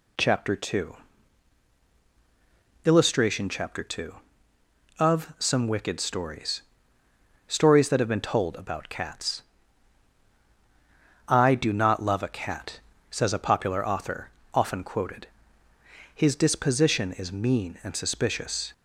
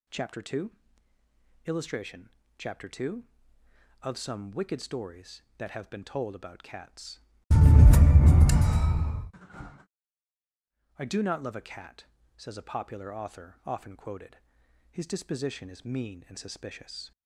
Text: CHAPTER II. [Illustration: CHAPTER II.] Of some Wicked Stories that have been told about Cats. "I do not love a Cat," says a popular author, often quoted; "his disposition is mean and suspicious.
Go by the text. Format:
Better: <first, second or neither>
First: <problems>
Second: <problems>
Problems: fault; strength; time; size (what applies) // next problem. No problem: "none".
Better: second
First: says "Stories" twice; at 7.4 s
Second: none